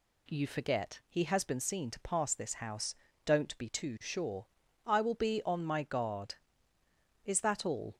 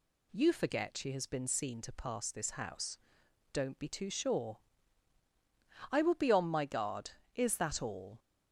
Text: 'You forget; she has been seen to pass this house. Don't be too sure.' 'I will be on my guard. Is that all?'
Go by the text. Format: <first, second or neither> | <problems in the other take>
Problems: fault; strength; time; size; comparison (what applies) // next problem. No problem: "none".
second | says "he" for "she"; at 1.0 s